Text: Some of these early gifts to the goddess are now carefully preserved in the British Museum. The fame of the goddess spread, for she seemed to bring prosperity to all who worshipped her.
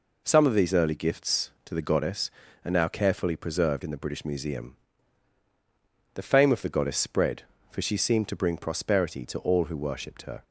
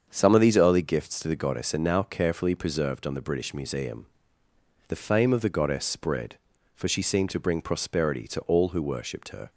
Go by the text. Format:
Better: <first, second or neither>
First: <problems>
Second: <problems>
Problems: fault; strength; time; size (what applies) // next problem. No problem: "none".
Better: first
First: none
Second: starts louder than the rest; strong; until 1.1 s; 7 dB // says "on" for "in"; at 3.0 s